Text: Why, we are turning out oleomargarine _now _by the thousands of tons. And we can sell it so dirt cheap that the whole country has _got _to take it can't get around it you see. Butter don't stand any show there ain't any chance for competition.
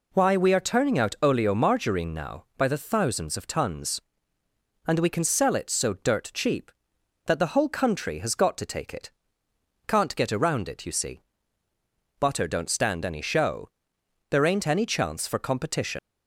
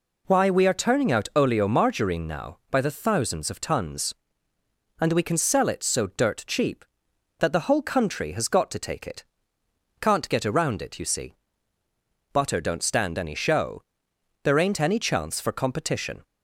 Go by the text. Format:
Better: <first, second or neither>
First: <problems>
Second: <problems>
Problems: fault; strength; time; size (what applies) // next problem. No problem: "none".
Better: second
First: pauses between "it" and "can't"; noticeable; at 9.1 s; 0.76 s long // pauses between "show" and "there"; noticeable; at 13.6 s; 0.62 s long // leaves "competition" unfinished; at 15.9 s; 105 ms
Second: pauses between "it" and "can't"; noticeable; at 9.2 s; 0.76 s long // pauses between "show" and "there"; noticeable; at 13.8 s; 0.62 s long